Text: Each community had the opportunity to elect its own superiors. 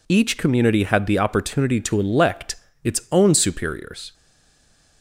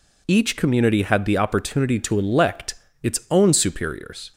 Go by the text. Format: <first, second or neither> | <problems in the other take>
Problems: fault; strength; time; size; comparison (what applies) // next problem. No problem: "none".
second | pauses between "elect" and "its"; slight; at 2.5 s; 0.28 s long; slight in the second // stays silent after the last word; slight; from 4.1 s on; 0.9 s long